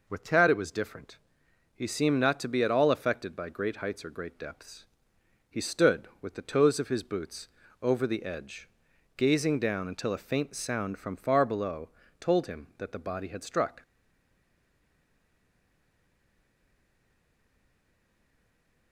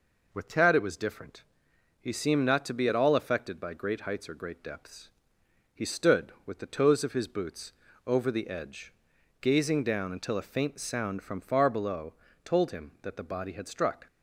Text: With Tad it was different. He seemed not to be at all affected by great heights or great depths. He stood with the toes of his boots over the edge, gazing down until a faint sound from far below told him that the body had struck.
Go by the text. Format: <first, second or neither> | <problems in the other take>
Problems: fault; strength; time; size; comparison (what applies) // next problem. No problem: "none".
second | pauses between "boots" and "over"; slight; at 7.4 s; 0.34 s long; slight in the second // pauses between "below" and "told"; slight; at 11.8 s; 0.32 s long; slight in the second // stays silent after the last word; strong; from 13.8 s on; 5.1 s long